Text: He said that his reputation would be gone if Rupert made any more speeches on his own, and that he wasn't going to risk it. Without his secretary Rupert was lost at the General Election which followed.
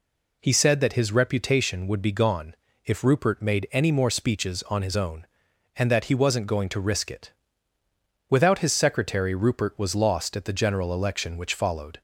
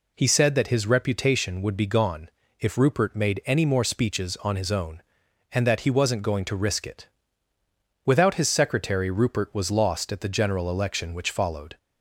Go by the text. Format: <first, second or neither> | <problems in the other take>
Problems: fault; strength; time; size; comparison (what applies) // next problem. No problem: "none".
neither | pauses between "gone" and "if"; slight; the same in both